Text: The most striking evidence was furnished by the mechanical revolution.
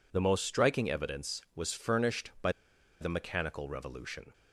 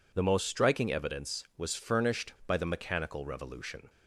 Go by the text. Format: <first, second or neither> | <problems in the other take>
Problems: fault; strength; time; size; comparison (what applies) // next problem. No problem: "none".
second | pauses between "by" and "the"; noticeable; at 2.5 s; 0.48 s long